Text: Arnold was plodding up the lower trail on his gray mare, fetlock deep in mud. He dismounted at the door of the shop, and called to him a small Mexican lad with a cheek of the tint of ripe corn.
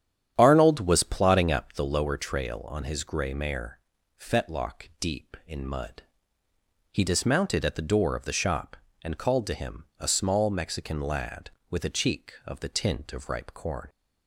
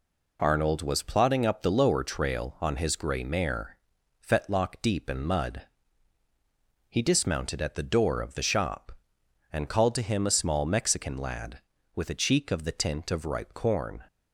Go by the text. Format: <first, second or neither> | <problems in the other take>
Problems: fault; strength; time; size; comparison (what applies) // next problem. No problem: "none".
second | starts louder than the rest; strong; until 2.0 s; 9 dB // pauses between "him" and "a"; slight; at 9.8 s; 0.16 s long